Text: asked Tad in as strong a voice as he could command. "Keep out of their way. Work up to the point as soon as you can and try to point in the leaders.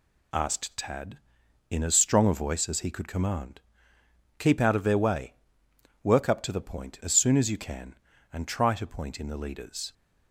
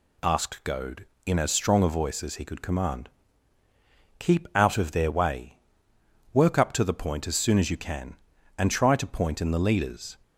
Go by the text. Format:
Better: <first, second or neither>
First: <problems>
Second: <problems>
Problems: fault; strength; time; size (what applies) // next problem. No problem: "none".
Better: first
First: none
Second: says "Goad" for "Tad"; at 0.6 s